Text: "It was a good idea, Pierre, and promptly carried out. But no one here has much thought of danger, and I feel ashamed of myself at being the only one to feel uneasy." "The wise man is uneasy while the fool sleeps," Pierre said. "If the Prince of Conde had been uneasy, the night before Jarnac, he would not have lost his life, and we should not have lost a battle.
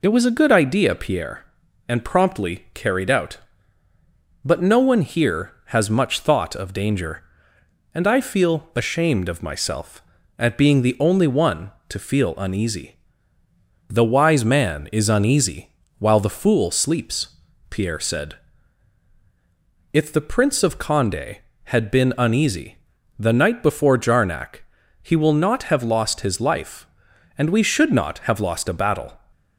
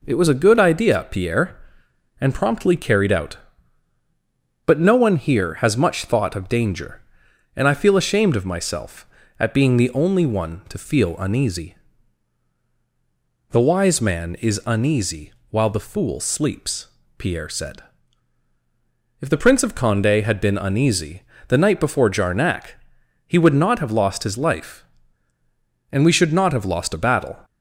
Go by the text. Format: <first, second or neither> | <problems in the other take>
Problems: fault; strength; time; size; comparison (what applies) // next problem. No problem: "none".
second | pauses between "uneasy" and "while"; slight; at 15.7 s; 0.28 s long; slight in the second // says "will" for "would"; at 25.1 s